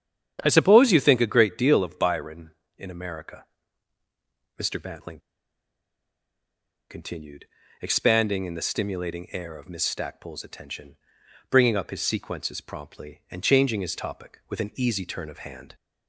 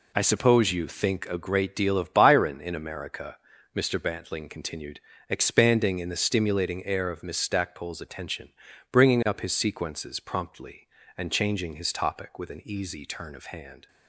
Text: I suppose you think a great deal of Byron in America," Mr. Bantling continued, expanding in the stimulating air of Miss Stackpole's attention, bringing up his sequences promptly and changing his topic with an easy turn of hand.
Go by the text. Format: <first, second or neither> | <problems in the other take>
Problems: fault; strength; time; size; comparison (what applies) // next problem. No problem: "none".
second | starts louder than the rest; strong; until 1.4 s; 9 dB // pauses between "Bantling" and "continued"; strong; at 5.1 s; 1.7 s long